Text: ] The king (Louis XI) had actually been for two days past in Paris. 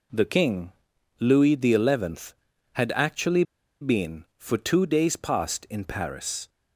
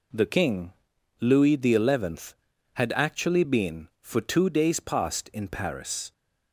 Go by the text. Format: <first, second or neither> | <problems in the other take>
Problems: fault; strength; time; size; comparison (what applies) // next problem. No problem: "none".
second | pauses between "actually" and "been"; at 3.4 s; 0.38 s long